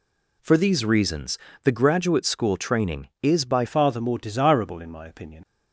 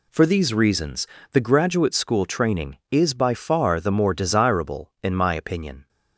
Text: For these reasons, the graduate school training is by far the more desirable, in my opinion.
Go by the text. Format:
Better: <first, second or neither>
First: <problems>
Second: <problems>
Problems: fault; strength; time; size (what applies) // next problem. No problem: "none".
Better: second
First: changes voice at "far"; from 3.6 s on; 1.8 s long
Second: none